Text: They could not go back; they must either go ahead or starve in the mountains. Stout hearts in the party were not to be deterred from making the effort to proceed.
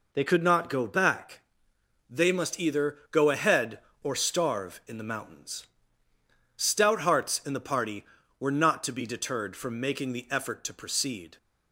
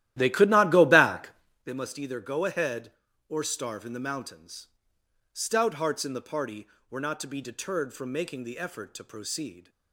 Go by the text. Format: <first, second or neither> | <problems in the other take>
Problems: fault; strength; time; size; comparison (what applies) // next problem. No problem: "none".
first | starts louder than the rest; strong; until 1.7 s; 13.5 dB